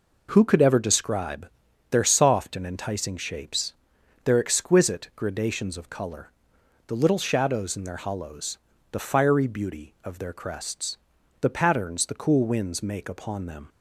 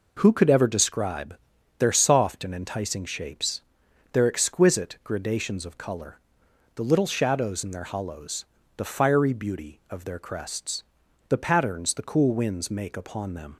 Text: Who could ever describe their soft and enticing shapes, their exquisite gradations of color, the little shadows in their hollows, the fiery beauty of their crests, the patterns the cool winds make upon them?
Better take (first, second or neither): neither